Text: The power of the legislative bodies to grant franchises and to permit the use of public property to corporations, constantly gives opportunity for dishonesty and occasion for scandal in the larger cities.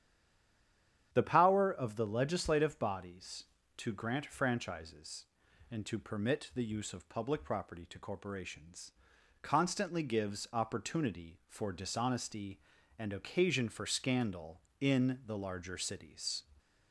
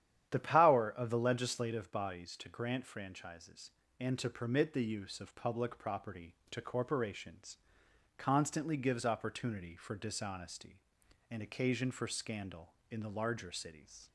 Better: second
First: stays silent before the first word; until 1.1 s; 1.1 s long // starts louder than the rest; strong; until 2.1 s; 10 dB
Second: starts louder than the rest; strong; until 1.3 s; 10.5 dB

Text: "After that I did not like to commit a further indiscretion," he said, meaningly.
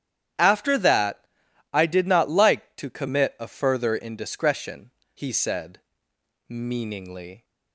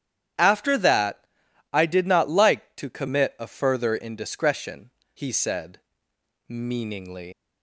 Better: first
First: starts louder than the rest; strong; until 1.8 s; 10.5 dB // pauses between "that" and "I"; noticeable; at 1.2 s; 0.48 s long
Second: starts louder than the rest; strong; until 1.8 s; 10.5 dB // pauses between "that" and "I"; noticeable; at 1.2 s; 0.48 s long // leaves "meaningly" unfinished; at 7.3 s; 110 ms

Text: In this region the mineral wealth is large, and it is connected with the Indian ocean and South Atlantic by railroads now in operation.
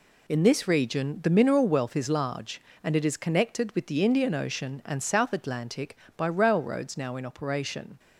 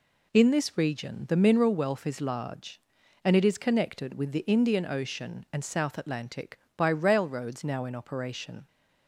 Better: neither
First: none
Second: none

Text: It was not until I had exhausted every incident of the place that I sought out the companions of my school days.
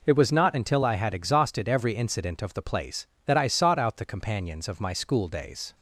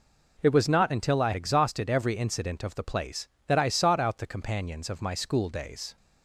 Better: first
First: none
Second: skips "had"; at 1.3 s

